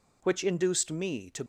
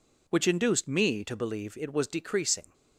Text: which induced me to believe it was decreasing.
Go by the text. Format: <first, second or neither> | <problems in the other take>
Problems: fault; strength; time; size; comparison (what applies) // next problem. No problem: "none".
second | stops before "believe it was decreasing"; at 1.4 s